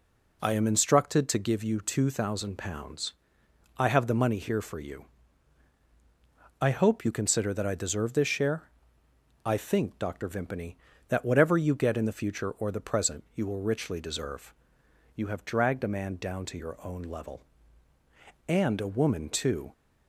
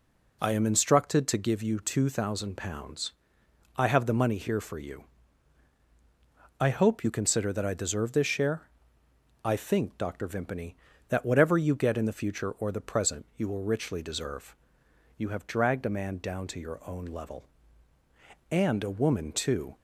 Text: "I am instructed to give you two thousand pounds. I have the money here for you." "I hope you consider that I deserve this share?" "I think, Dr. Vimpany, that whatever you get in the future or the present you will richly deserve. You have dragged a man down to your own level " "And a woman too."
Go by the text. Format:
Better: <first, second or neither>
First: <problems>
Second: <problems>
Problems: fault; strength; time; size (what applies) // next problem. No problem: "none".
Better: neither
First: none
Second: none